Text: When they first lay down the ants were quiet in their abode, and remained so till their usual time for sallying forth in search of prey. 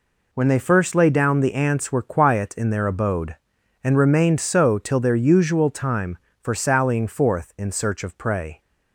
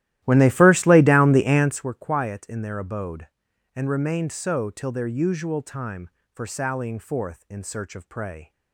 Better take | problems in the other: first | starts louder than the rest; strong; until 1.9 s; 14.5 dB

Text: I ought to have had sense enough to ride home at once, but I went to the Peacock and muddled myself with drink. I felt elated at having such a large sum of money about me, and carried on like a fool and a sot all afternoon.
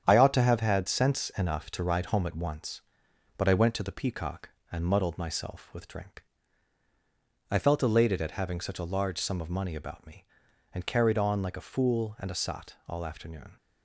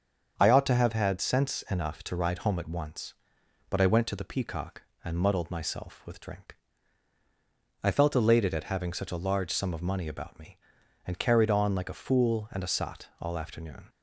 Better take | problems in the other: second | gets quieter; throughout; 6.5 dB // starts louder than the rest; strong; until 1.0 s; 9 dB; strong in the second

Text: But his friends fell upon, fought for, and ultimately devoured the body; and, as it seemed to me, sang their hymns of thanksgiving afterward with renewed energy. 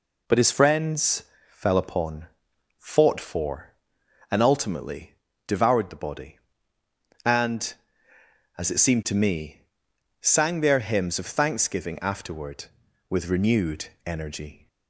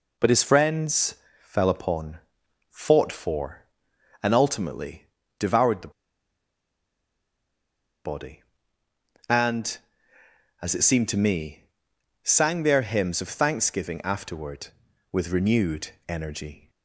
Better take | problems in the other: first | pauses between "friends" and "fell"; slight; at 1.1 s; 0.26 s long; slight in the first // pauses between "ultimately" and "devoured"; slight; at 5.0 s; 0.34 s long; slight in the first // pauses between "the" and "body"; strong; at 5.9 s; 2.1 s long // pauses between "renewed" and "energy"; slight; at 15.8 s; 0.18 s long; slight in the first

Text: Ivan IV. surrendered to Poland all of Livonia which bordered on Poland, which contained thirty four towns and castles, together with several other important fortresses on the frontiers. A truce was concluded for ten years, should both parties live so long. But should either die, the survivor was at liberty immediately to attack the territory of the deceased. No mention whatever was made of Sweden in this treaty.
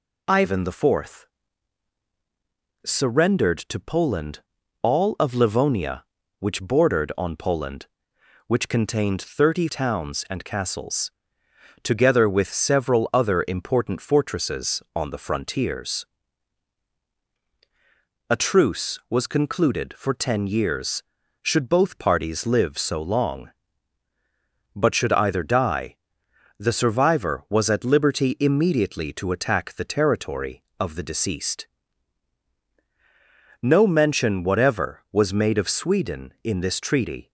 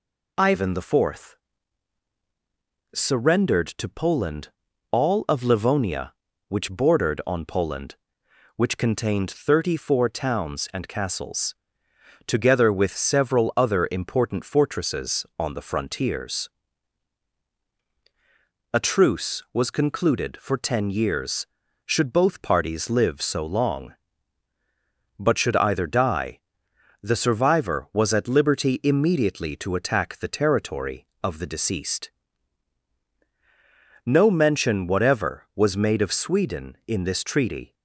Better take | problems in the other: second | pauses between "Poland" and "all"; at 4.4 s; 0.40 s long; also in the second // skips "four"; at 9.6 s

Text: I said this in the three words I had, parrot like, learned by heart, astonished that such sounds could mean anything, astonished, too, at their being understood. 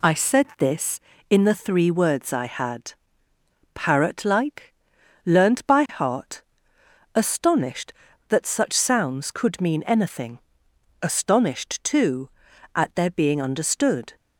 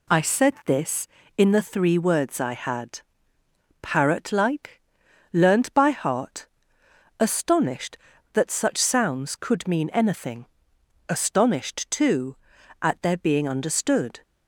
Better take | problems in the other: neither | none

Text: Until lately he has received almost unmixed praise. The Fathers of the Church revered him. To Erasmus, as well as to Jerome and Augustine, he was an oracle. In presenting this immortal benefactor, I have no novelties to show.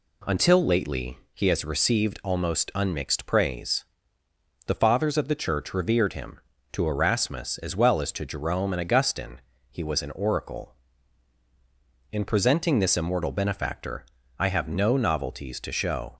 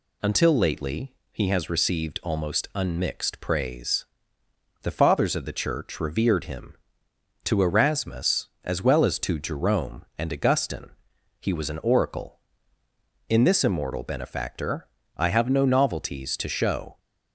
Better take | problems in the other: first | pauses between "lately" and "he"; slight; at 1.1 s; 0.18 s long; slight in the first // skips "presenting"; at 13.4 s

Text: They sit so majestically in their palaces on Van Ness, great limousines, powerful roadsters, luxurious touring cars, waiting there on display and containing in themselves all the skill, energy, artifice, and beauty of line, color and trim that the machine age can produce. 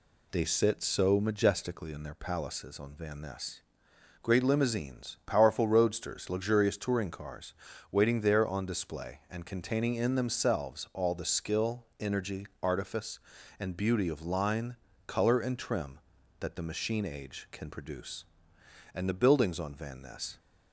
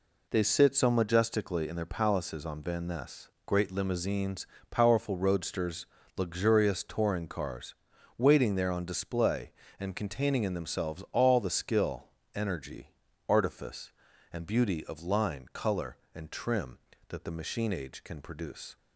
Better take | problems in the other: second | goes on to say "And the buildings on Van Ness"; from 18.9 s on; 1.4 s long

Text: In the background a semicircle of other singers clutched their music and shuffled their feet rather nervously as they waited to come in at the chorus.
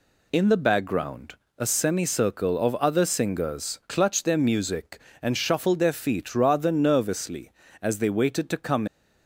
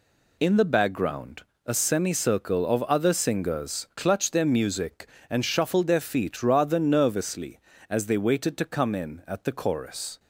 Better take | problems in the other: second | pauses between "background" and "a"; slight; at 1.3 s; 0.24 s long; slight in the second // stops before "in at the chorus"; at 8.8 s

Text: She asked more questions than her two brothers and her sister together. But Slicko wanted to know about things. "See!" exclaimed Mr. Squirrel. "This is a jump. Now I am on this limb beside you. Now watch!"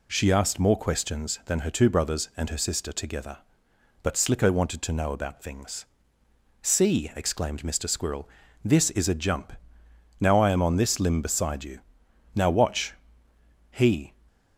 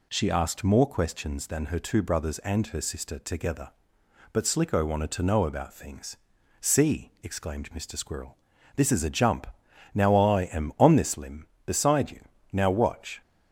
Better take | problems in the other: second | goes on to say "He"; slight; from 13.7 s on; 0.42 s long

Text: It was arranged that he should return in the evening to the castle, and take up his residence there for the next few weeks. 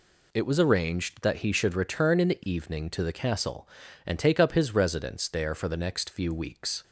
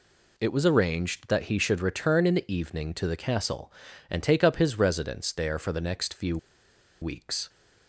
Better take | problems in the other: first | pauses between "few" and "weeks"; noticeable; at 6.3 s; 0.64 s long

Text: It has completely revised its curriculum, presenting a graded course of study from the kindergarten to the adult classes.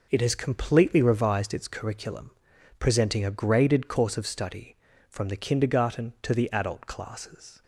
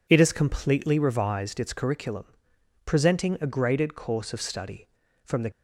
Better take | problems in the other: first | stops before "kindergarten to the adult classes"; at 5.5 s

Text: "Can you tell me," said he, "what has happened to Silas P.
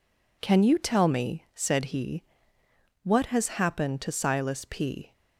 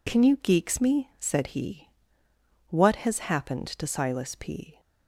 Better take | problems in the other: first | says "geeks" for "tell"; at 0.3 s

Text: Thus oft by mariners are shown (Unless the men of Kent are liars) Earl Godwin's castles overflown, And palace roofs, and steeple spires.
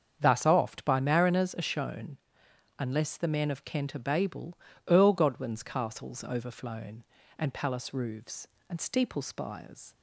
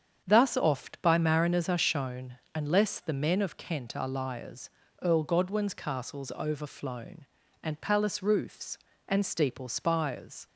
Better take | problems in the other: second | starts louder than the rest; strong; until 1.2 s; 7.5 dB; strong in the second // says "babel" for "liars"; at 4.0 s

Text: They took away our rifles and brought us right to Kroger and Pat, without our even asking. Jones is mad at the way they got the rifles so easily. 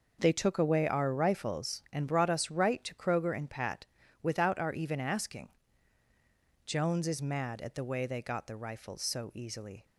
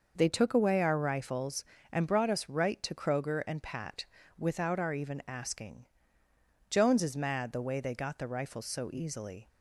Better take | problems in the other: first | skips "at"; at 7.5 s

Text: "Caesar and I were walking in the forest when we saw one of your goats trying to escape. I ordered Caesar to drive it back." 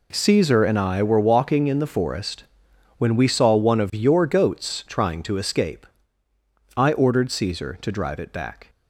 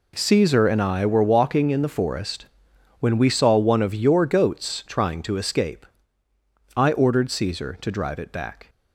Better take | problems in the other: neither | pauses between "forest" and "when"; noticeable; the same in both

